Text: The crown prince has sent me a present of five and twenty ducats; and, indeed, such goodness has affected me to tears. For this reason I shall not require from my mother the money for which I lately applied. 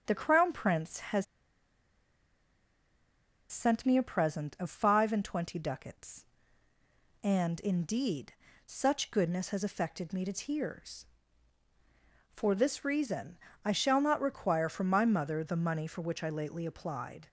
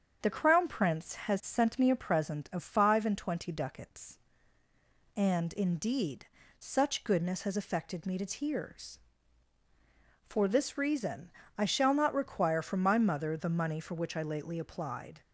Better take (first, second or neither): second